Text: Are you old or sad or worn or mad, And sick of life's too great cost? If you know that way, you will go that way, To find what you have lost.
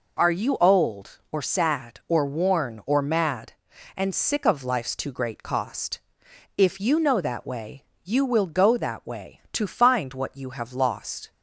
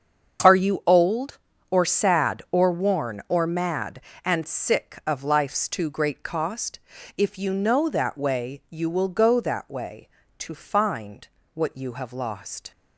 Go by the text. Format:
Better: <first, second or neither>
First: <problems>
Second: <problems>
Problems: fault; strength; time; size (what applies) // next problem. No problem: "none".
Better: first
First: none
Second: gets quieter; strong; throughout; 13 dB // pauses between "find" and "what"; slight; at 11.2 s; 0.26 s long